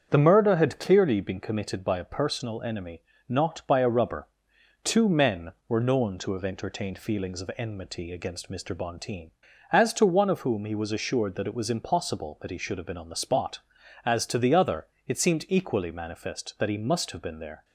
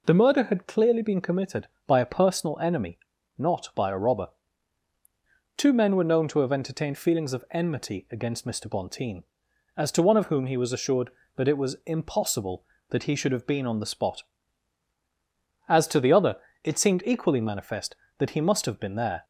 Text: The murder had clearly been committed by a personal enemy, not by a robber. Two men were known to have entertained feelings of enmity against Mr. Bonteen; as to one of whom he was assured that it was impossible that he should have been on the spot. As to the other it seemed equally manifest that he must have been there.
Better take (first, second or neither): second